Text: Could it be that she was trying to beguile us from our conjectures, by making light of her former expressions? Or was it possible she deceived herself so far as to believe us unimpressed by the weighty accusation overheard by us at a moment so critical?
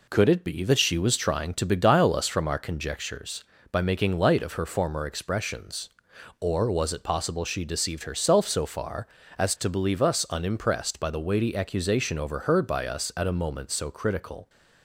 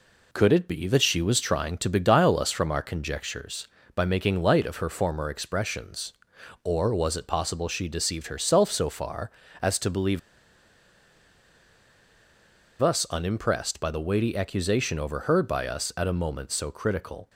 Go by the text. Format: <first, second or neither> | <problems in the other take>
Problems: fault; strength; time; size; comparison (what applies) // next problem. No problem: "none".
first | pauses between "believe" and "us"; strong; at 10.1 s; 2.6 s long